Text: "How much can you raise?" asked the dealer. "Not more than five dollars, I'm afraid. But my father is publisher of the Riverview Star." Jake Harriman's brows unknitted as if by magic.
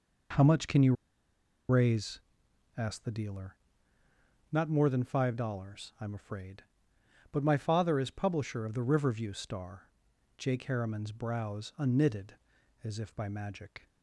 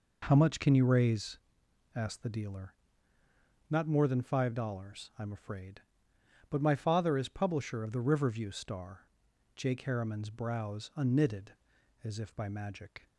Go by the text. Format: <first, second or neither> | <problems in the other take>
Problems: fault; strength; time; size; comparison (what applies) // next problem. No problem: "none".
second | pauses between "you" and "raise"; noticeable; at 0.9 s; 0.75 s long